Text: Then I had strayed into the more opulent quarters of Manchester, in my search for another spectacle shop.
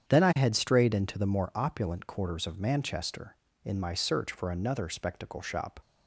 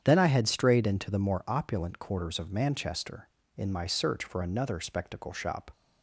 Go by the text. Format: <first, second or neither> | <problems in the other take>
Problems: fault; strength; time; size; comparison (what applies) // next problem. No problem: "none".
neither | starts louder than the rest; strong; the same in both